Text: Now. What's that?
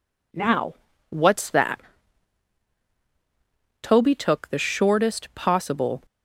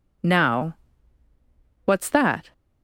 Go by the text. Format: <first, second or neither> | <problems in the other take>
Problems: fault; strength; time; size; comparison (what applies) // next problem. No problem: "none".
second | goes on to say "Toby took the shortest possible"; strong; from 3.8 s on; 2.2 s long